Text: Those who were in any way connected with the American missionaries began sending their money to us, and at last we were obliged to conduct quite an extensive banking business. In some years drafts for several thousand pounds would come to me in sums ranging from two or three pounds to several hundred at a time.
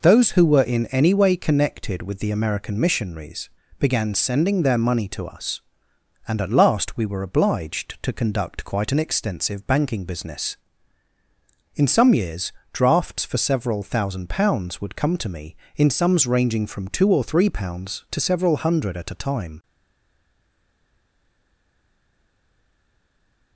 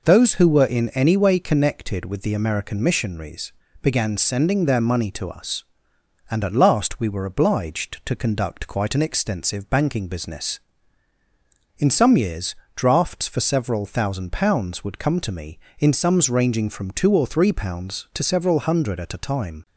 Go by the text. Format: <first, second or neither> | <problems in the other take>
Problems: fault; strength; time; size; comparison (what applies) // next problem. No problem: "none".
second | pauses between "missionaries" and "began"; slight; at 3.5 s; 0.30 s long; slight in the second // pauses between "years" and "drafts"; slight; at 12.5 s; 0.20 s long; slight in the second // stays silent after the last word; strong; from 19.6 s on; 3.9 s long